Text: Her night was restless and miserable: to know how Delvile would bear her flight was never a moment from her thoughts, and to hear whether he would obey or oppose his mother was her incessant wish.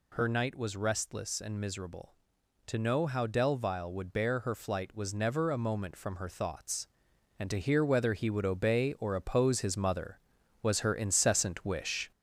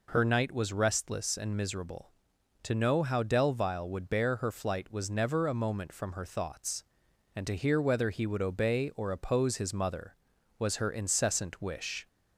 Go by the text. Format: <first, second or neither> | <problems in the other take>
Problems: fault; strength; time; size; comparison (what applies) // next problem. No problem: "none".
second | gets louder; throughout; 3.5 dB